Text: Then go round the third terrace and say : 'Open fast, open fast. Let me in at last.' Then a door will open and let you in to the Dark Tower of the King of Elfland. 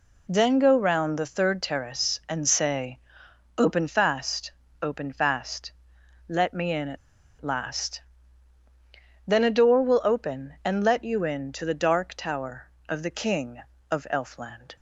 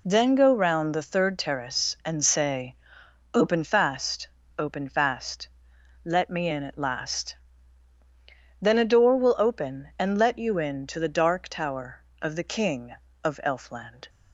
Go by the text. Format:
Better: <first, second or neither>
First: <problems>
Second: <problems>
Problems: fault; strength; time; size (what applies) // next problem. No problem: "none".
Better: second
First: pauses between "at" and "last"; at 6.9 s; 0.43 s long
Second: none